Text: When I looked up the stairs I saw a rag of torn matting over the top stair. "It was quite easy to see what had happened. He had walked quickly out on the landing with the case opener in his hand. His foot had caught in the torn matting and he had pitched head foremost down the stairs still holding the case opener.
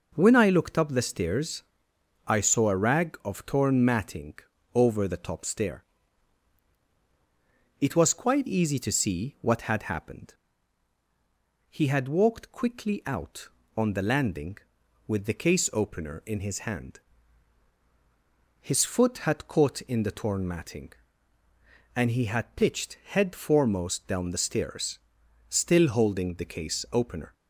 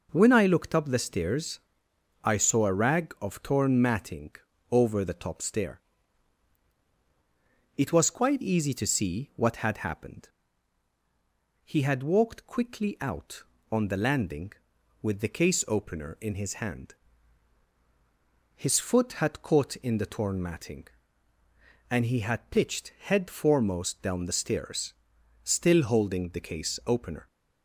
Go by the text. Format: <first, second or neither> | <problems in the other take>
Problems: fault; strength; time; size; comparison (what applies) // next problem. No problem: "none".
neither | pauses between "stairs" and "I"; noticeable; the same in both // pauses between "matting" and "over"; slight; the same in both // pauses between "stairs" and "still"; noticeable; the same in both